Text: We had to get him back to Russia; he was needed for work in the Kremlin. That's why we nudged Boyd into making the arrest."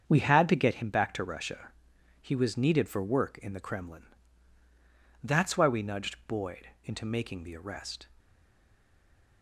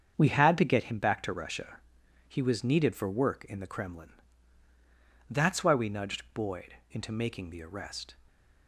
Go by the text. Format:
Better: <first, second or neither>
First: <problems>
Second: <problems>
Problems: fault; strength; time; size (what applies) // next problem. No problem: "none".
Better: second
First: starts louder than the rest; strong; until 1.0 s; 7 dB // pauses between "Boyd" and "into"; slight; at 6.6 s; 0.16 s long // stays silent after the last word; noticeable; from 8.1 s on; 1.3 s long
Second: starts louder than the rest; strong; until 1.1 s; 7 dB // pauses between "Boyd" and "into"; slight; at 6.7 s; 0.16 s long